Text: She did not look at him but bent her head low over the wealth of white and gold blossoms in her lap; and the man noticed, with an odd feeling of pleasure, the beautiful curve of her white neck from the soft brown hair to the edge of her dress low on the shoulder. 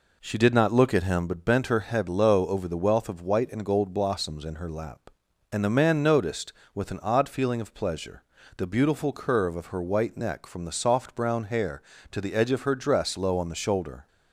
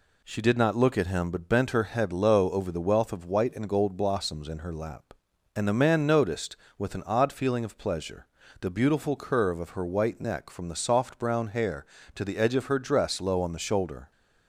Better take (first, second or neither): second